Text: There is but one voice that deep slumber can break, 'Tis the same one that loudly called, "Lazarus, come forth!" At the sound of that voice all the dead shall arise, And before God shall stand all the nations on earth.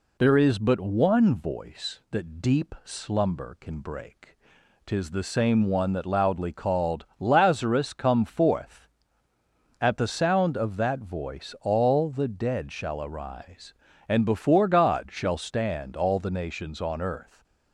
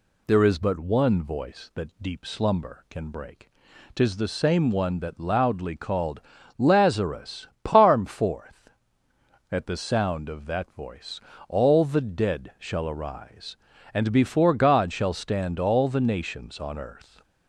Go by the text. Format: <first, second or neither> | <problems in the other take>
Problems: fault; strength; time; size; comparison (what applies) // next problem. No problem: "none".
first | says "parm" for "come"; at 7.6 s // pauses between "voice" and "all"; slight; at 11.1 s; 0.30 s long